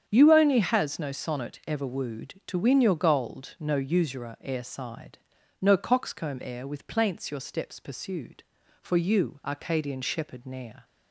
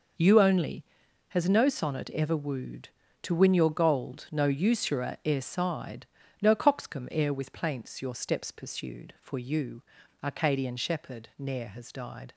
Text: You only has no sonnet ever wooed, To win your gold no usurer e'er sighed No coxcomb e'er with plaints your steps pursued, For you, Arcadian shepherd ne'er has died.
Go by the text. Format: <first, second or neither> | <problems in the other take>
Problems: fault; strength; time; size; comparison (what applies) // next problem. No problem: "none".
second | starts louder than the rest; strong; until 1.0 s; 8.5 dB // pauses between "sighed" and "No"; at 5.1 s; 0.42 s long; slight in the second // stops before "has died"; at 10.8 s